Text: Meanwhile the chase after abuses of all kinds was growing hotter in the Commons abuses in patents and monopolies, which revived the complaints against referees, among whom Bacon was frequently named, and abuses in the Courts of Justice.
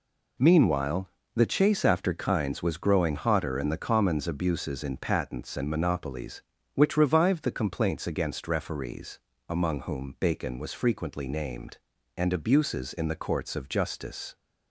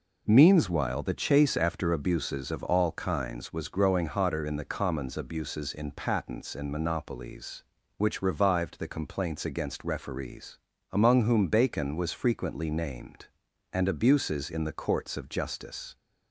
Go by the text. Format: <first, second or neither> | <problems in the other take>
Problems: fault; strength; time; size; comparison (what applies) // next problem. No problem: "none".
second | pauses between "Meanwhile" and "the"; slight; at 1.0 s; 0.28 s long // skips "abuses of all"; at 2.1 s